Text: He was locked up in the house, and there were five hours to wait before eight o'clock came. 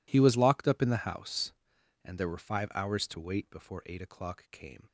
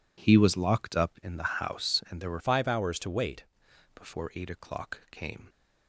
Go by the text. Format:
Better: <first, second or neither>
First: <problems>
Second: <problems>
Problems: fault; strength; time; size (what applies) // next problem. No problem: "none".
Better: first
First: none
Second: changes voice from "five" to "wait"; from 2.3 to 3.4 s; 1.1 s long